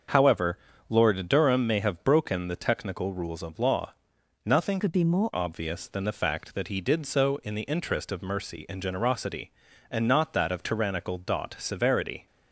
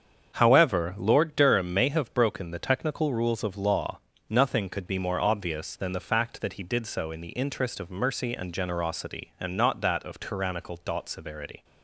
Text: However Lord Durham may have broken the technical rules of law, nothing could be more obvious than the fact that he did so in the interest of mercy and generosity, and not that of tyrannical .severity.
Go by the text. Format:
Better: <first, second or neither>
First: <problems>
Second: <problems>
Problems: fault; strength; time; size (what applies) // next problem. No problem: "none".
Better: second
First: starts louder than the rest; until 1.4 s; 7 dB // pauses between "However" and "Lord"; slight; at 0.5 s; 0.32 s long // changes voice from "could" to "more"; from 4.7 to 5.3 s; 0.6 s long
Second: starts louder than the rest; strong; until 1.3 s; 7 dB